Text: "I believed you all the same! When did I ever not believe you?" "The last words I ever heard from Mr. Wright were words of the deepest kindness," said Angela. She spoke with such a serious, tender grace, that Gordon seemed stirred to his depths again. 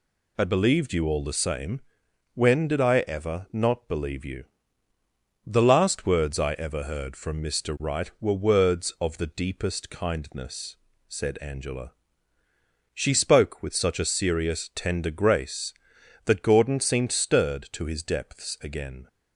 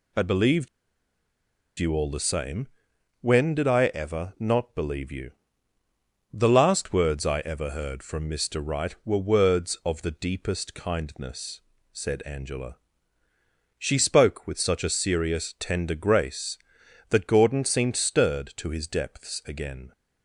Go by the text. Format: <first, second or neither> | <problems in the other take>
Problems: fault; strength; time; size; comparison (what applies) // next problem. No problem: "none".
first | pauses between "believed" and "you"; at 0.6 s; 1.1 s long